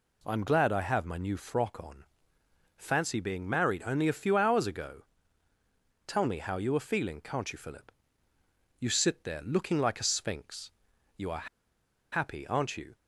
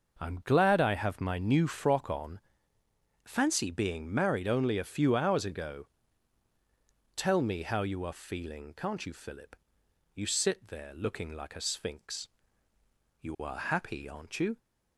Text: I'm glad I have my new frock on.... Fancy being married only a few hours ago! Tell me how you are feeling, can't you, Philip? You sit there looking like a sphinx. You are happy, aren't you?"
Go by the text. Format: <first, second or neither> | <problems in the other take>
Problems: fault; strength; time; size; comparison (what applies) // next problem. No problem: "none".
second | pauses between "are" and "happy"; noticeable; at 11.4 s; 0.65 s long